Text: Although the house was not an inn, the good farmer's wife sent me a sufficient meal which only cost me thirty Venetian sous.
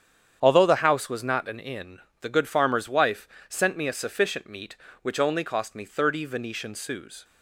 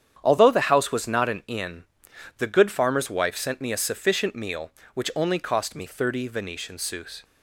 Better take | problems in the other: second | starts louder than the rest; strong; until 1.4 s; 8.5 dB; strong in the second // pauses between "wife" and "sent"; slight; at 3.2 s; 0.22 s long // says "meat" for "meal"; at 4.4 s

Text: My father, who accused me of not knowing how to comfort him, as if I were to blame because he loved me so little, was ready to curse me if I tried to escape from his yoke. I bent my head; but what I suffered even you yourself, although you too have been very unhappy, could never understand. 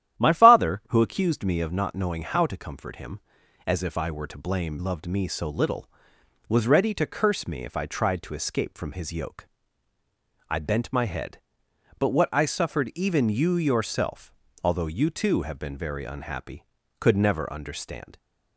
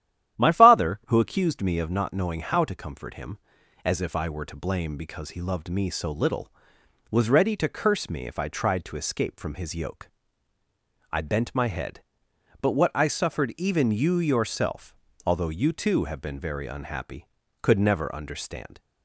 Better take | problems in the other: second | starts louder than the rest; strong; until 1.2 s; 11.5 dB; strong in the second // skips "because he"; at 4.7 s

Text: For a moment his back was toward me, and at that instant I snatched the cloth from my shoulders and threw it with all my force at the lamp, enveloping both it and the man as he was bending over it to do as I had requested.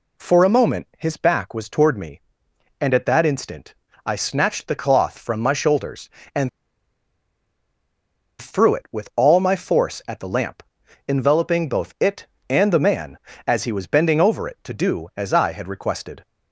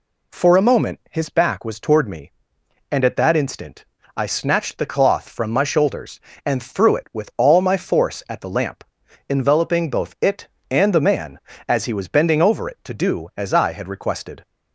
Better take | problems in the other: second | pauses between "instant" and "I"; slight; at 3.7 s; 0.32 s long; slight in the second // pauses between "and" and "threw"; strong; at 6.4 s; 1.9 s long

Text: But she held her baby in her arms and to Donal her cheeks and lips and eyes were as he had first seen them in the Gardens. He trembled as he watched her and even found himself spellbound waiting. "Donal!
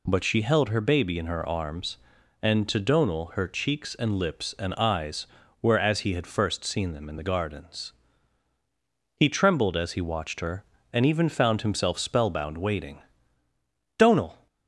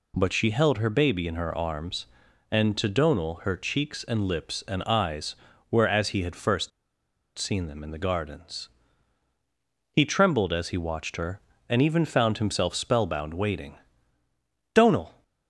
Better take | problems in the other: first | pauses between "first" and "seen"; noticeable; at 6.7 s; 0.68 s long

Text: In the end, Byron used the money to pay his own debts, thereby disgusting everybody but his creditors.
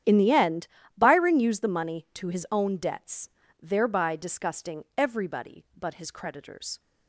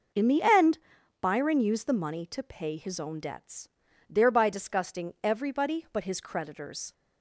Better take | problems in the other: second | starts louder than the rest; strong; until 1.3 s; 10 dB // skips "pay"; at 2.2 s

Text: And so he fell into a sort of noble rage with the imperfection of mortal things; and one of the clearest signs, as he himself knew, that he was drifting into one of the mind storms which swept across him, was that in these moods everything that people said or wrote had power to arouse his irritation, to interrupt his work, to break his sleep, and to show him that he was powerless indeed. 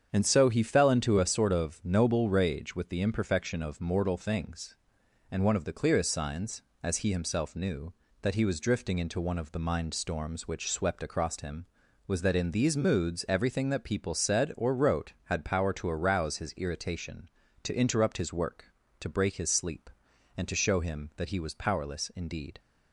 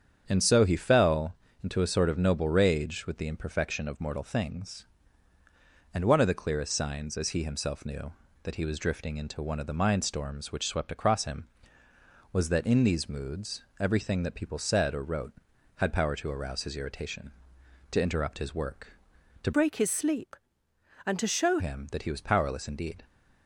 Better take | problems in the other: first | starts louder than the rest; strong; until 1.2 s; 7.5 dB; strong in the first // pauses between "fell" and "into"; slight; at 1.3 s; 0.28 s long // pauses between "moods" and "everything"; slight; at 13.6 s; 0.16 s long // changes voice from "break" to "show"; from 19.5 to 21.5 s; 2.0 s long

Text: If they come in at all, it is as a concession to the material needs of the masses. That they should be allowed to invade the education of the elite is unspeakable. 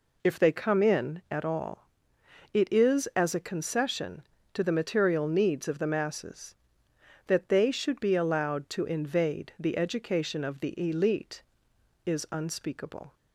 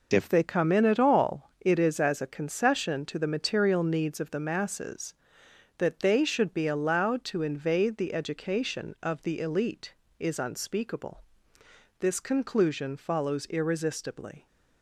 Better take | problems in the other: first | goes on to say "This conclusion follows irresistibly"; strong; from 11.9 s on; 2.4 s long

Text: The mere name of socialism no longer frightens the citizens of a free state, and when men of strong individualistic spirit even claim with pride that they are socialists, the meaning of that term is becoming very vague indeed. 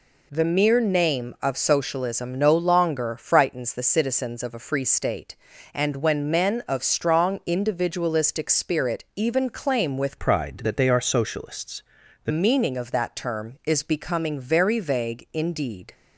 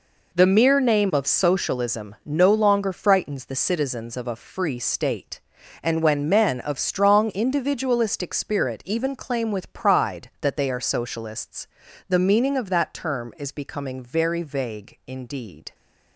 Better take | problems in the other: second | changes voice from "pride" to "the"; from 10.1 to 12.3 s; 2.2 s long

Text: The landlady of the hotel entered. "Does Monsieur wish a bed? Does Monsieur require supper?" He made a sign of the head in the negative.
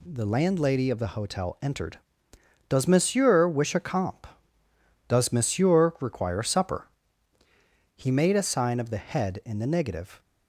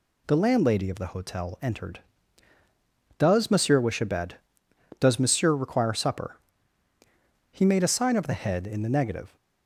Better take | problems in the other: second | says "comp" for "bed"; at 3.7 s

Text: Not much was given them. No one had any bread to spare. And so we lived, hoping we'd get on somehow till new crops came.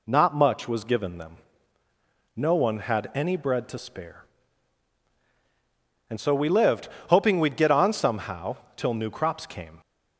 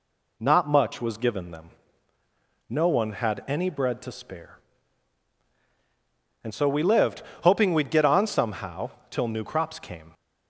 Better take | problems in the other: neither | pauses between "somehow" and "till"; slight; the same in both

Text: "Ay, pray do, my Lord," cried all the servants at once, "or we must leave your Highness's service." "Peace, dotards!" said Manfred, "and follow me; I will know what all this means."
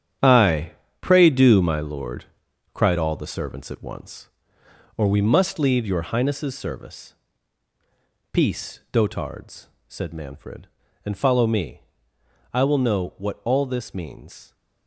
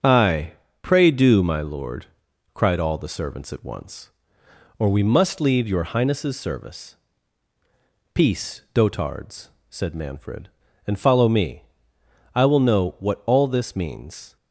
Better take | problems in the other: second | gets quieter; strong; throughout; 11 dB // starts louder than the rest; strong; until 1.5 s; 9 dB; also in the second

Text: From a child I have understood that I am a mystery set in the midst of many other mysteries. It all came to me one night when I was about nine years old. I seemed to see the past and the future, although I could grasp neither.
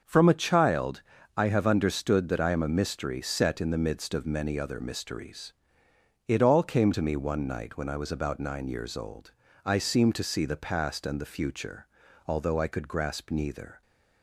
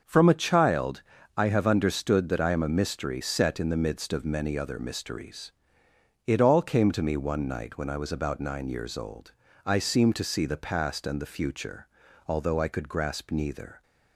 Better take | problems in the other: neither | starts louder than the rest; the same in both // pauses between "child" and "I"; slight; the same in both

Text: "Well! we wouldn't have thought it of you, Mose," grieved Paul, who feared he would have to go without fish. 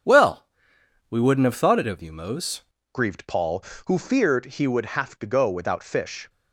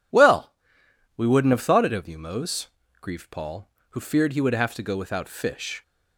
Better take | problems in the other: second | starts louder than the rest; strong; until 1.7 s; 7.5 dB // changes voice at "grieved"; from 2.9 s on; 3.3 s long

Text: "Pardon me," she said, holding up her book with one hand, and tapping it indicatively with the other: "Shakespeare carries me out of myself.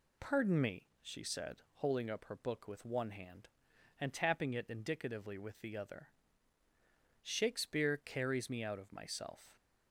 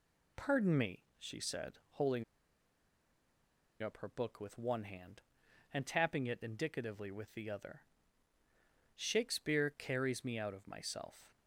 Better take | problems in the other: first | pauses between "holding" and "up"; strong; at 2.2 s; 1.5 s long

